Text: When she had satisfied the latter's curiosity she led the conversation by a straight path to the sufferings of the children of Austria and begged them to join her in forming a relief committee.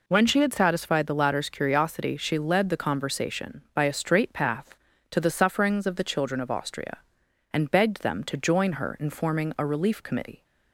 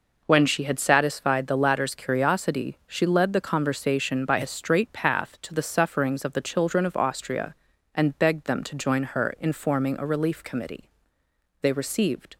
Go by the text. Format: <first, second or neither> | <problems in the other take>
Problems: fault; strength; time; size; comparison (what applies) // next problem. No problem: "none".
first | goes on to say "They received"; noticeable; from 11.6 s on; 0.76 s long